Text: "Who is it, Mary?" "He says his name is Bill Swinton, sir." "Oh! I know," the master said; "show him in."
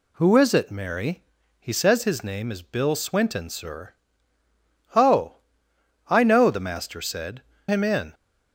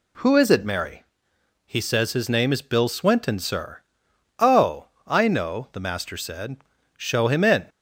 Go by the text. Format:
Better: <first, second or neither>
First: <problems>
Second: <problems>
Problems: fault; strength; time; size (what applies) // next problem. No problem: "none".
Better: second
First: skips "show"; at 7.5 s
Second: none